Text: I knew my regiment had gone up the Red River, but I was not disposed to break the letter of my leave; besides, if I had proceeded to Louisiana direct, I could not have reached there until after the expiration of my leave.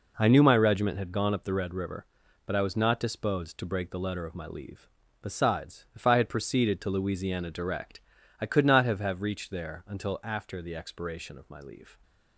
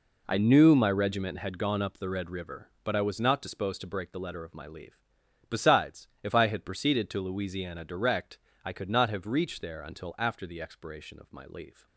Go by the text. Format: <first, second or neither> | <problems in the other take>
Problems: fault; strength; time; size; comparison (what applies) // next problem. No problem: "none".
second | says "have" twice; at 8.9 s